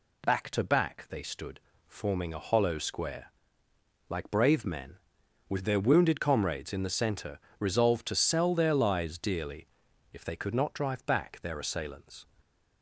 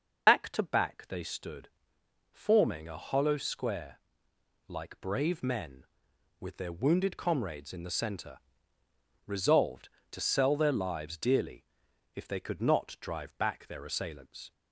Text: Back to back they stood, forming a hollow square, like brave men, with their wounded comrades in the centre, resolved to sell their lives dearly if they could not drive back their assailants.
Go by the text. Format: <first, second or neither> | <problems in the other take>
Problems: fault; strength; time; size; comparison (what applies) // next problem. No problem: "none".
first | loses the start of "Back"; at 0.2 s; 50 ms // starts louder than the rest; noticeable; until 1.3 s; 6 dB // pauses between "dearly" and "if"; noticeable; at 11.6 s; 0.50 s long; noticeable in the first